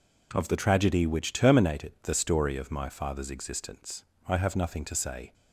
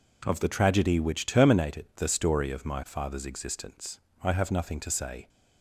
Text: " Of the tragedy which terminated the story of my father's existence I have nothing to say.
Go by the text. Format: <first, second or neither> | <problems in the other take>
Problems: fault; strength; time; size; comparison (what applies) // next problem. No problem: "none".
neither | pauses between "existence" and "I"; slight; the same in both